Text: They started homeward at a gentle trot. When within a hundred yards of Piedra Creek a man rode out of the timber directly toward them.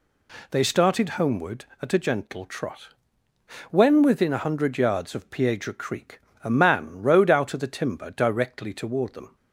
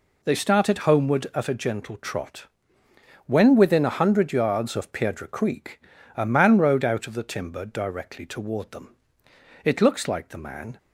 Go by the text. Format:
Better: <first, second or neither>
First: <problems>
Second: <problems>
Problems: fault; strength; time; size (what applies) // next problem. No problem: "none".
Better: first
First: pauses between "Creek" and "a"; slight; at 6.2 s; 0.24 s long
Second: pauses between "Creek" and "a"; slight; at 5.7 s; 0.34 s long // goes on to say "It looks like the man"; noticeable; from 9.6 s on; 1.1 s long